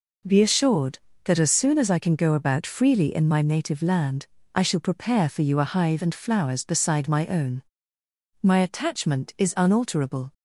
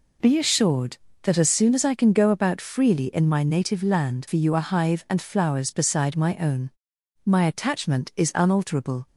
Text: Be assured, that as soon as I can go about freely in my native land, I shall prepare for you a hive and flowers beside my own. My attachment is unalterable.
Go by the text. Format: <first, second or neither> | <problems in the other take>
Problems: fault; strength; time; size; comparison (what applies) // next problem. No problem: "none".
first | skips "I shall prepare"; at 4.2 s